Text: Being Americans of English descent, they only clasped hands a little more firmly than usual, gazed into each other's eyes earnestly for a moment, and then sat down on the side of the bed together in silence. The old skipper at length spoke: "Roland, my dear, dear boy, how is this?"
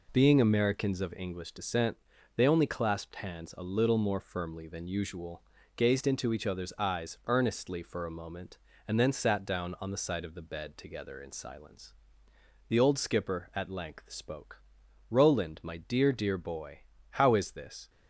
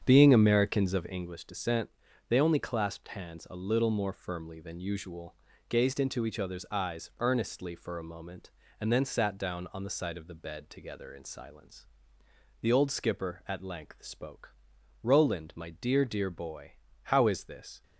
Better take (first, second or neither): first